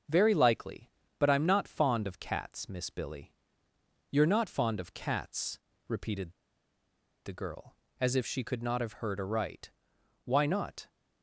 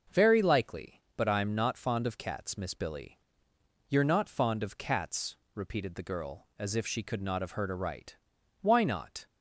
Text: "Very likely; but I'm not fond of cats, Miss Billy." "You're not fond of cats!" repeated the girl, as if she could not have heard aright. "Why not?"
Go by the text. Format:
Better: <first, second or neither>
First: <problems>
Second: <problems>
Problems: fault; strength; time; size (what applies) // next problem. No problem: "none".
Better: second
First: starts louder than the rest; until 1.3 s; 6.5 dB // pauses between "repeated" and "the"; noticeable; at 6.3 s; 0.92 s long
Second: starts louder than the rest; noticeable; until 1.2 s; 6 dB